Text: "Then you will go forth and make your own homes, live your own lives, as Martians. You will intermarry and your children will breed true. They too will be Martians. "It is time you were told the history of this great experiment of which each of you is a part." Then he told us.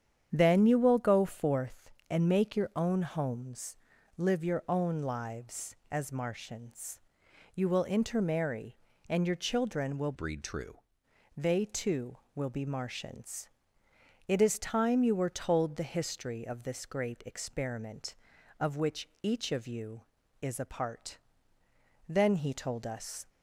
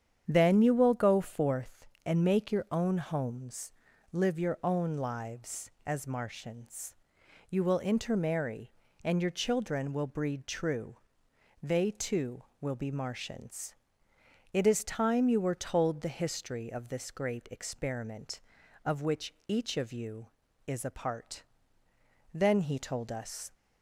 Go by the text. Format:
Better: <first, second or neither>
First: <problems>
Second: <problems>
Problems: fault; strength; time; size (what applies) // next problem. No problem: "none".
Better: second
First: starts louder than the rest; strong; until 1.3 s; 8.5 dB // changes voice from "breed" to "true"; from 10.1 to 10.8 s; 0.7 s long // pauses between "which" and "each"; slight; at 19.0 s; 0.16 s long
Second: starts louder than the rest; strong; until 1.2 s; 8.5 dB // pauses between "which" and "each"; slight; at 19.3 s; 0.16 s long